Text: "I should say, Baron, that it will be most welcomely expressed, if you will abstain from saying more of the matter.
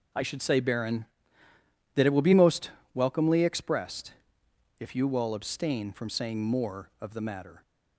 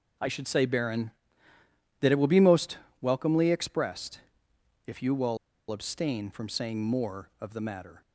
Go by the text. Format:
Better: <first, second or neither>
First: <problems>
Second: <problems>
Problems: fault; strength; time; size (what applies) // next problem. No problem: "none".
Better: first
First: pauses between "most" and "welcomely"; slight; at 2.7 s; 0.22 s long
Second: pauses between "most" and "welcomely"; slight; at 2.7 s; 0.22 s long // pauses between "will" and "abstain"; slight; at 5.3 s; 0.33 s long